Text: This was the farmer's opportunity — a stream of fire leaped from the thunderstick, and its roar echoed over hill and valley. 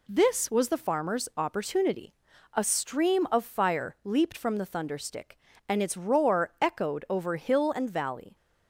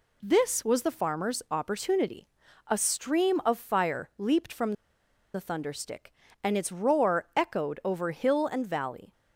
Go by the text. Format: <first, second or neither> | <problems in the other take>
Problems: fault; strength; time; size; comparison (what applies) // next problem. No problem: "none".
first | pauses between "from" and "the"; noticeable; at 4.7 s; 0.61 s long